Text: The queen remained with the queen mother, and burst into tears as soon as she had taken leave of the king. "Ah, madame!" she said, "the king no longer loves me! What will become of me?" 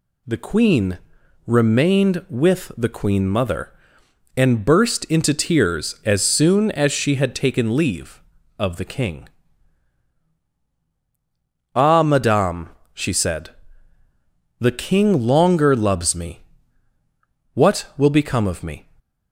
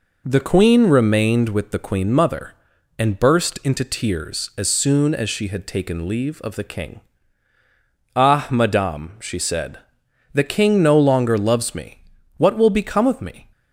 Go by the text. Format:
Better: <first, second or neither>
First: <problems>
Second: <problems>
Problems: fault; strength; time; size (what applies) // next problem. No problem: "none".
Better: second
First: pauses between "queen" and "remained"; noticeable; at 0.9 s; 0.48 s long // skips "no"; at 15.2 s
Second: none